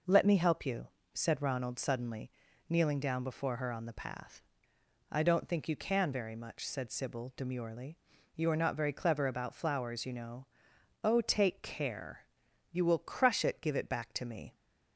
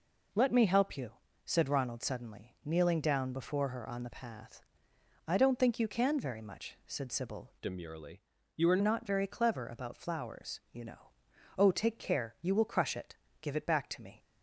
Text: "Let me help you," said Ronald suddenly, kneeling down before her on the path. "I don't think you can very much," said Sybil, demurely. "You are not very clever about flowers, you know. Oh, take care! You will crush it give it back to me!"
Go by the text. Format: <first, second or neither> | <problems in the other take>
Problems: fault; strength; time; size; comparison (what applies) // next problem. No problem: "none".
first | changes voice from "demurely" to "are"; from 7.6 to 8.8 s; 1.2 s long // pauses between "it" and "give"; slight; at 13.1 s; 0.24 s long